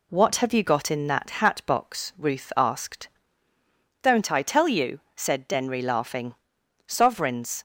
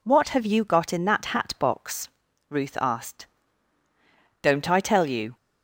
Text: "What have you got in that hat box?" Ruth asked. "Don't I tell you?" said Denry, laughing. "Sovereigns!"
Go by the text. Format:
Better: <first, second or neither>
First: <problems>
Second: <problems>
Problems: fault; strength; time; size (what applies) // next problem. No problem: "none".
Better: first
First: none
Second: stops before "said Denry laughing Sovereigns"; at 5.3 s